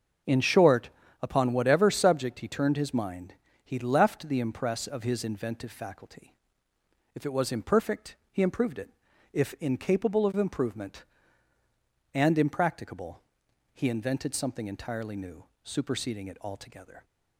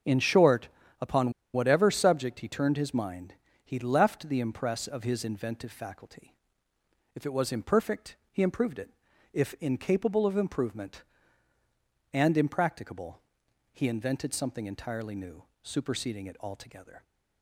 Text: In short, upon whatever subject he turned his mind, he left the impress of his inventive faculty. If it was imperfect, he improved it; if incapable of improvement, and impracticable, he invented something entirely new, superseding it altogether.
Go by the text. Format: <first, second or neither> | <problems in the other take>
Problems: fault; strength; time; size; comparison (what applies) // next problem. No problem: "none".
first | starts louder than the rest; until 1.6 s; 6.5 dB; also in the first // pauses between "upon" and "whatever"; slight; at 1.3 s; 0.22 s long